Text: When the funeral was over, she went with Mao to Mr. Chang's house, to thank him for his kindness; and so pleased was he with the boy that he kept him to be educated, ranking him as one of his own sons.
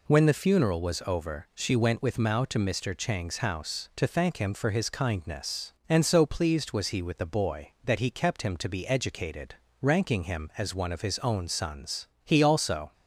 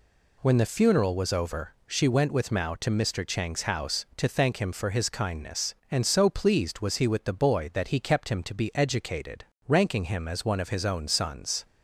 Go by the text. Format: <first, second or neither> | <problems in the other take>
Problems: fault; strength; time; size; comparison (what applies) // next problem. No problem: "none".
second | goes on to say "He also"; noticeable; from 12.2 s on; 0.68 s long